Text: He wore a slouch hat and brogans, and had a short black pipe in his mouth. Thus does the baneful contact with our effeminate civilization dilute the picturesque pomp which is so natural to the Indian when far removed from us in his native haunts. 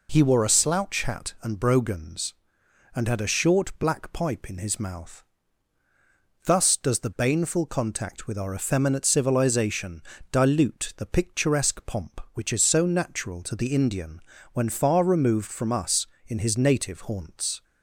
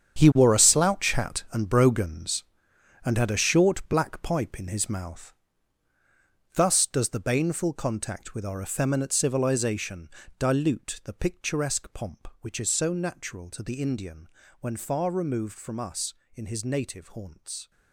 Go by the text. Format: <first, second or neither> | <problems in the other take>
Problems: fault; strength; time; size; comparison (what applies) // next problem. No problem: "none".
first | gets quieter; strong; throughout; 13 dB // pauses between "civilization" and "dilute"; slight; at 10.1 s; 0.28 s long; slight in the first // pauses between "Indian" and "when"; slight; at 14.2 s; 0.34 s long; slight in the first